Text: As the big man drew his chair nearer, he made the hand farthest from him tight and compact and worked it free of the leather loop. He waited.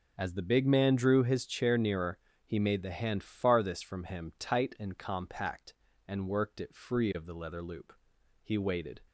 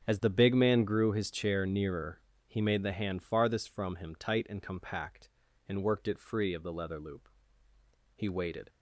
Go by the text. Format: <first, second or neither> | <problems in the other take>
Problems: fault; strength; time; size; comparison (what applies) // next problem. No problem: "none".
first | starts louder than the rest; until 1.0 s; 7 dB // says "grew" for "drew"; at 0.8 s